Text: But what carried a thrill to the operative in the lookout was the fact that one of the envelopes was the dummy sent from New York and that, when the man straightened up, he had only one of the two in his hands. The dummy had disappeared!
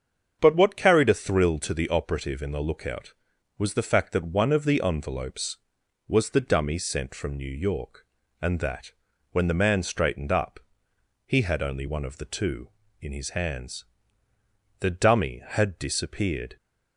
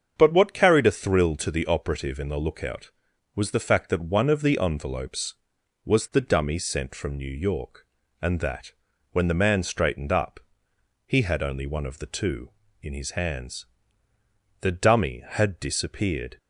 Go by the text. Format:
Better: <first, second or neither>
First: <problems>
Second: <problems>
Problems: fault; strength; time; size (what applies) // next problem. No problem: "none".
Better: neither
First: starts louder than the rest; strong; until 1.4 s; 7 dB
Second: starts louder than the rest; strong; until 1.1 s; 7 dB